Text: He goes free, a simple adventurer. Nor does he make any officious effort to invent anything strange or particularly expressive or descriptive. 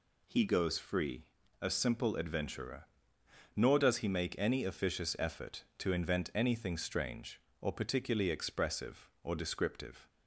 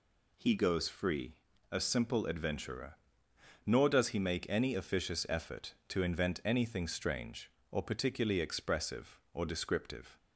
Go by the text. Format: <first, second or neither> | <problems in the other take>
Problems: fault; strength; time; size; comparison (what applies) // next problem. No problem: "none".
neither | none